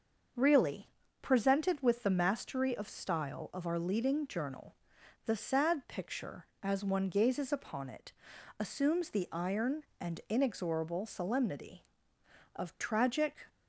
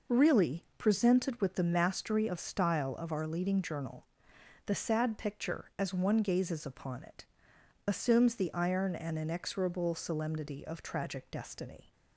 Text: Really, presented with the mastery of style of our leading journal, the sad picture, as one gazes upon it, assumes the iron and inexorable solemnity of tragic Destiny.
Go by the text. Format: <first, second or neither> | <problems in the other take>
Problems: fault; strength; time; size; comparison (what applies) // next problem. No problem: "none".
second | starts louder than the rest; until 1.6 s; 6.5 dB // stops before "Destiny"; at 13.4 s